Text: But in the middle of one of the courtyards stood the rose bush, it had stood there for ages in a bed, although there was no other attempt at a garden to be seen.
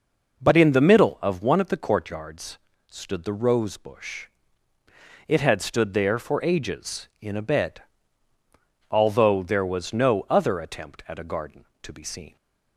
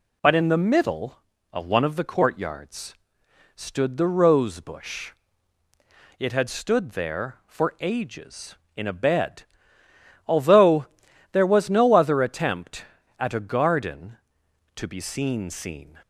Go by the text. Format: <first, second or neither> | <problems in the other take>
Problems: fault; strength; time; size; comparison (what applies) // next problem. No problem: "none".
first | pauses between "courtyards" and "stood"; noticeable; at 2.9 s; 0.62 s long; slight in the first // pauses between "although" and "there"; at 10.8 s; 0.44 s long // says "seen" twice; at 15.4 s